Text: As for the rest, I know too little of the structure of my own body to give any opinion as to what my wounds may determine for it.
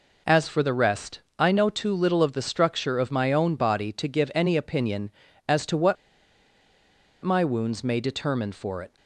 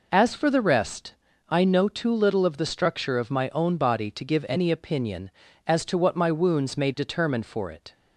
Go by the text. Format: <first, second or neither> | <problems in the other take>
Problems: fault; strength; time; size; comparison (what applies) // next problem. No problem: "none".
second | pauses between "what" and "my"; strong; at 5.9 s; 1.2 s long